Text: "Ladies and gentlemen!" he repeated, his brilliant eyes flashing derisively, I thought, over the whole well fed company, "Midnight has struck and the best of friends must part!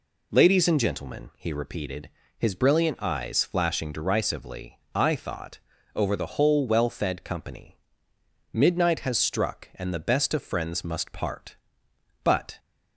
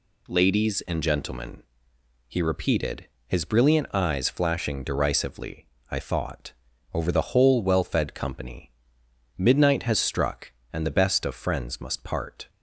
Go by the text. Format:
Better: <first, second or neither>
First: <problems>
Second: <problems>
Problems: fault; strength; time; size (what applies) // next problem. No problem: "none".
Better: second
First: goes on to say "But"; slight; from 12.2 s on; 0.36 s long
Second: none